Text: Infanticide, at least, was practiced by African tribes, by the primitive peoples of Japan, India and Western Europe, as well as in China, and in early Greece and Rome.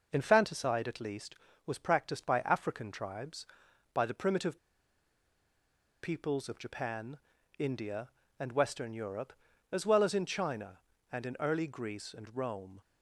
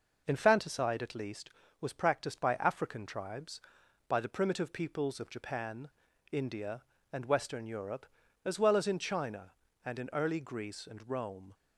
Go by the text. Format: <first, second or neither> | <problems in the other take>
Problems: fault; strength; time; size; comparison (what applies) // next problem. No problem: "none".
second | pauses between "primitive" and "peoples"; strong; at 4.5 s; 1.4 s long